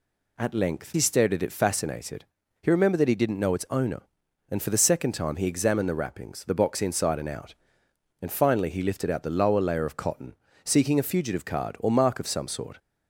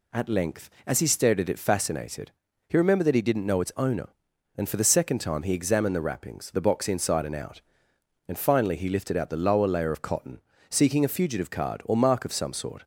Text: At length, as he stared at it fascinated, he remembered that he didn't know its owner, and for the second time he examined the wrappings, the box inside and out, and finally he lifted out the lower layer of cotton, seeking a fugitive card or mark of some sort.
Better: second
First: skips "as"; at 0.9 s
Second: none

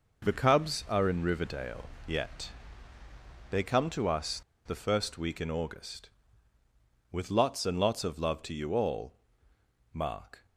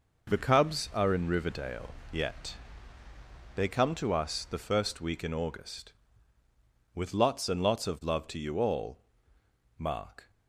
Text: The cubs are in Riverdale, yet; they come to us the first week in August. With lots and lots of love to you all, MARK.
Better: second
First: pauses between "us" and "the"; slight; at 4.4 s; 0.26 s long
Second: none

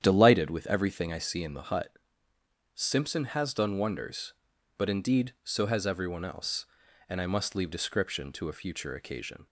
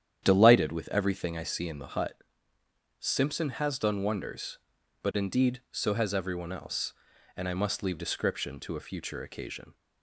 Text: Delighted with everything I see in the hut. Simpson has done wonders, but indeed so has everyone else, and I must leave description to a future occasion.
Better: neither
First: starts louder than the rest; strong; until 1.0 s; 9.5 dB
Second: starts louder than the rest; strong; until 1.2 s; 9.5 dB

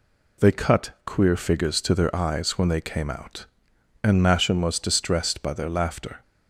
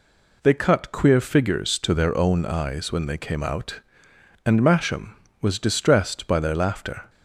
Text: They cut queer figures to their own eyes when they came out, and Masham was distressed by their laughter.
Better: second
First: skips "own"; at 2.1 s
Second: none

